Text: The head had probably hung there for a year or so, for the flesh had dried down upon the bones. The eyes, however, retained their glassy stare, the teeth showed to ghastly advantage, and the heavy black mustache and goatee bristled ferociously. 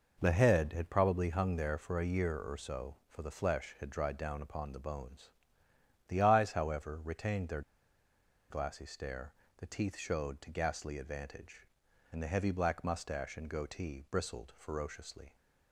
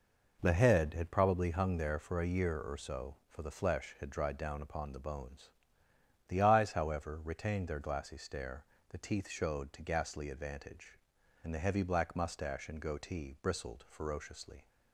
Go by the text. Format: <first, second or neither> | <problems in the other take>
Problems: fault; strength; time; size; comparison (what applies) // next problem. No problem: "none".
second | pauses between "their" and "glassy"; noticeable; at 7.6 s; 0.89 s long